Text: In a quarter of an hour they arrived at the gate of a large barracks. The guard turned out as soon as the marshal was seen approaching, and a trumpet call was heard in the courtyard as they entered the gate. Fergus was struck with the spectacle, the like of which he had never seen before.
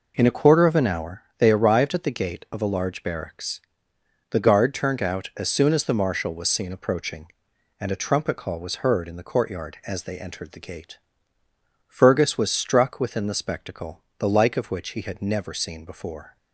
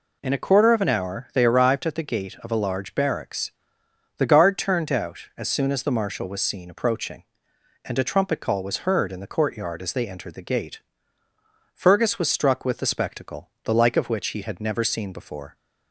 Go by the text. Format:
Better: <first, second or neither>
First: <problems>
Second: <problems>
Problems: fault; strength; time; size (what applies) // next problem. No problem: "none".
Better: second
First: pauses between "hour" and "they"; slight; at 1.2 s; 0.16 s long // says "within" for "with"; at 13.0 s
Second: none